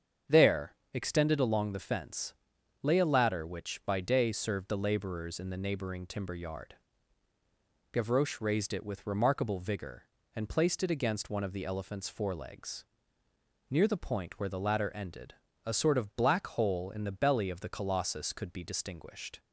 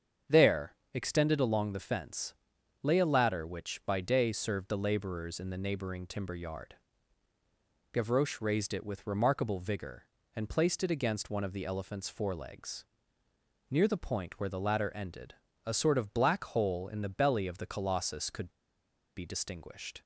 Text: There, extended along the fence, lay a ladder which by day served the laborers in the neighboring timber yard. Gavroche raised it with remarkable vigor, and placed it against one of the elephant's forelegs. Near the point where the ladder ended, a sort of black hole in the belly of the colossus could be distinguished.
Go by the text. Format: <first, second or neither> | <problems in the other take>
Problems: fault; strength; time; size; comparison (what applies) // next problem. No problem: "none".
first | starts louder than the rest; strong; until 1.4 s; 7.5 dB; strong in the first // pauses between "could" and "be"; noticeable; at 18.4 s; 0.67 s long